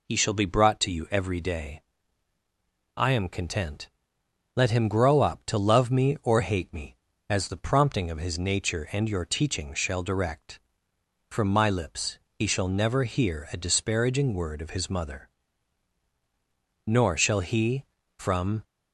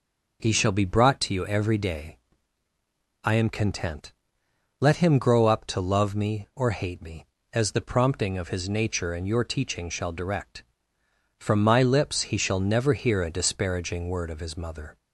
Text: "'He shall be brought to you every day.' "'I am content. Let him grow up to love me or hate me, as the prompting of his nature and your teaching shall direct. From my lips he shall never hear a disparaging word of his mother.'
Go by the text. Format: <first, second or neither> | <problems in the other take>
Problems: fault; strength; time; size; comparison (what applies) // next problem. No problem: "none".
second | pauses between "lips" and "he"; slight; at 12.1 s; 0.16 s long // goes on to say "Nor shall he from"; strong; from 16.8 s on; 1.7 s long